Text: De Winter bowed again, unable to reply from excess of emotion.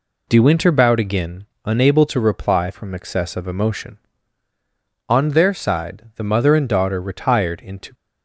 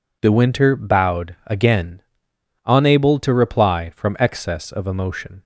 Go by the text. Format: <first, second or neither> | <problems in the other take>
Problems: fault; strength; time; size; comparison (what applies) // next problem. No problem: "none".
second | goes on to say "On their side the mother and daughter retired into"; strong; from 5.0 s on; 2.8 s long